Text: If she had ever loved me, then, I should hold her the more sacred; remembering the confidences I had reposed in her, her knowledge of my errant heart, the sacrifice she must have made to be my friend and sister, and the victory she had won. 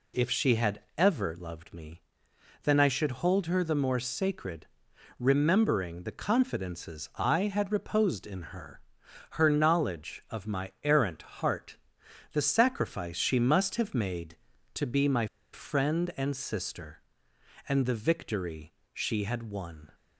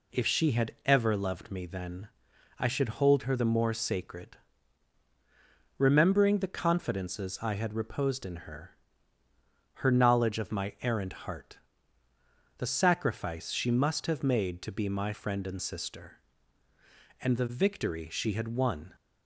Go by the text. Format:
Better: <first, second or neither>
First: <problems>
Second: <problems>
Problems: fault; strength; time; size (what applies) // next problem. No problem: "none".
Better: second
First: pauses between "had" and "ever"; slight; at 0.7 s; 0.18 s long // pauses between "my" and "friend"; slight; at 15.2 s; 0.26 s long // pauses between "victory" and "she"; slight; at 18.7 s; 0.22 s long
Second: none